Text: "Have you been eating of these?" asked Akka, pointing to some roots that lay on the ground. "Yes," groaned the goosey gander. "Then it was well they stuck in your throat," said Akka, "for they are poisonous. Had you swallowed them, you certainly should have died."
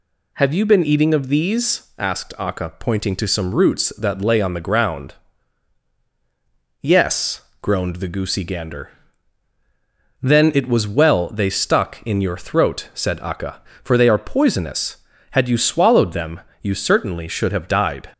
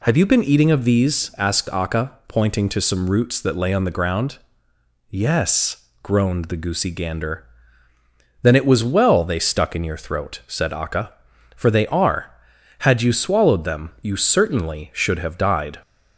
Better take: first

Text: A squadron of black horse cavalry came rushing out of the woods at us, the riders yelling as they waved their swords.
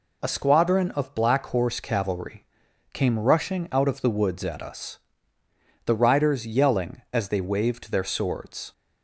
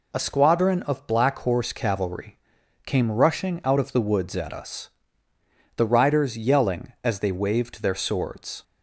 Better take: neither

